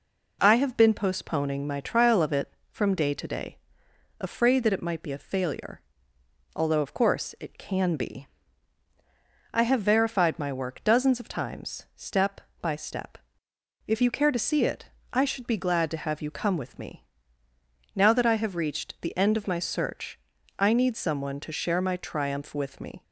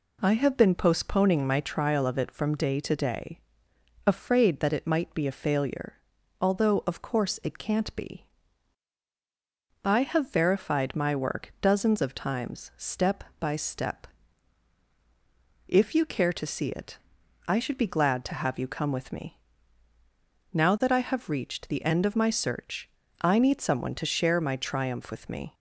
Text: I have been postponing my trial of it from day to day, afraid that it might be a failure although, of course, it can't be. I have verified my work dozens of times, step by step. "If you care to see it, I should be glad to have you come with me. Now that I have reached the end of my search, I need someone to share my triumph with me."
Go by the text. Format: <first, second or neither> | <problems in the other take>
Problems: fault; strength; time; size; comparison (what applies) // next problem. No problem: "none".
second | pauses between "failure" and "although"; noticeable; at 5.8 s; 0.74 s long; noticeable in the second // says "can" for "can't"; at 7.5 s